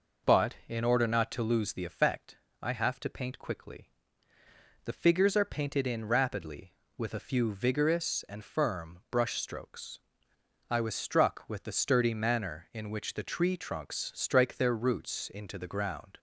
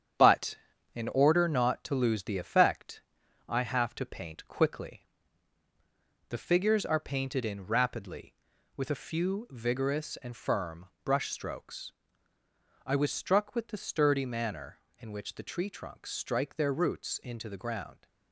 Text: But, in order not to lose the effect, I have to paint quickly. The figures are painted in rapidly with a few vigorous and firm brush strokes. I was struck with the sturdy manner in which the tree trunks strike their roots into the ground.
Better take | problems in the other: first | gets quieter; noticeable; throughout; 6 dB // pauses between "firm" and "brush"; slight; at 10.8 s; 0.16 s long

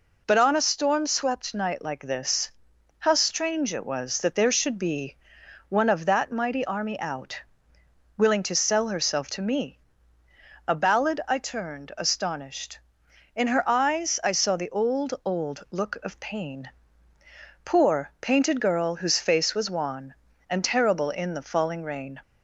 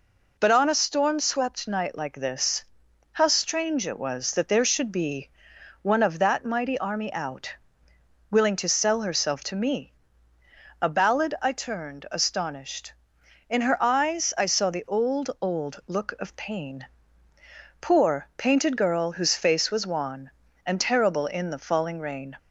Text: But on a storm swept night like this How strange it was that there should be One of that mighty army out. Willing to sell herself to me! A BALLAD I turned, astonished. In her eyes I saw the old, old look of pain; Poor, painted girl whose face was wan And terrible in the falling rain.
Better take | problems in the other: neither | pauses between "this" and "How"; noticeable; the same in both // pauses between "be" and "One"; noticeable; the same in both

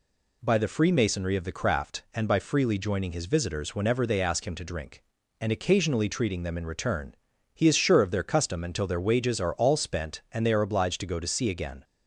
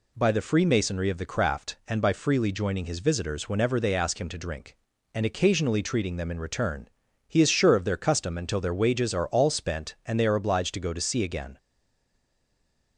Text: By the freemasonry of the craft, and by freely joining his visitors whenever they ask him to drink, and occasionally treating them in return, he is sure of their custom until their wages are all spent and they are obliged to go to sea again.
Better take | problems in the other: first | stays silent after the last word; noticeable; from 11.5 s on; 1.4 s long

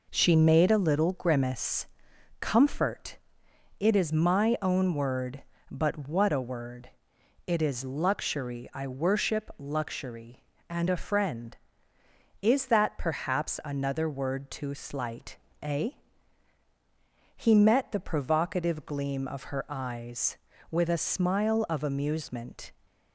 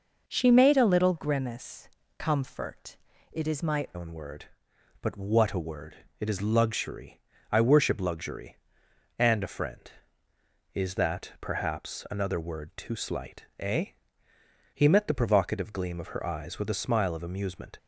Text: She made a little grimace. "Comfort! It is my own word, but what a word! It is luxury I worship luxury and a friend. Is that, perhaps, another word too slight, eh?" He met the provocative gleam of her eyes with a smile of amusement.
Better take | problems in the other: first | changes voice at "own"; from 3.9 s on; 13.8 s long // pauses between "luxury" and "I"; slight; at 7.2 s; 0.28 s long

